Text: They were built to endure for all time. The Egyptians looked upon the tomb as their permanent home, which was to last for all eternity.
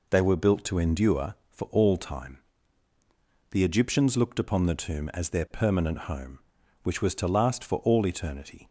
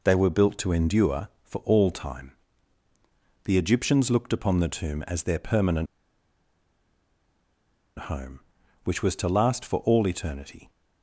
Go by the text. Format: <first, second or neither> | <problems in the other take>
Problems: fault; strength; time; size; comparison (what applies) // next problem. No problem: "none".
first | pauses between "permanent" and "home"; strong; at 5.8 s; 2.1 s long